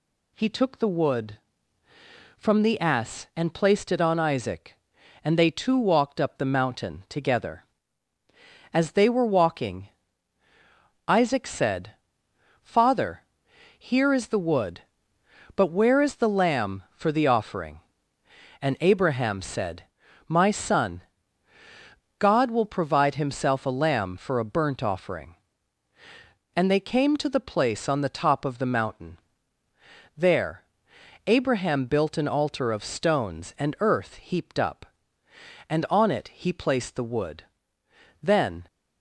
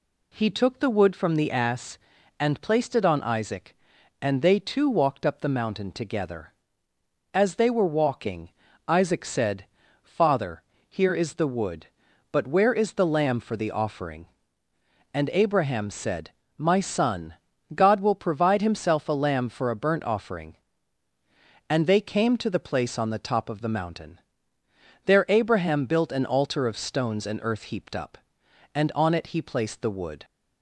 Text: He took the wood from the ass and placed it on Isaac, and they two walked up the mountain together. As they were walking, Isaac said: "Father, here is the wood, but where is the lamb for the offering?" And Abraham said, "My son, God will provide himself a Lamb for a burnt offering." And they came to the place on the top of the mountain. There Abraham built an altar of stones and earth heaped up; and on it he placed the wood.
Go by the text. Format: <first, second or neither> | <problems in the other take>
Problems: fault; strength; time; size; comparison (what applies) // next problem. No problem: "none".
second | pauses between "There" and "Abraham"; noticeable; at 30.6 s; 0.64 s long // goes on to say "Then"; slight; from 38.2 s on; 0.42 s long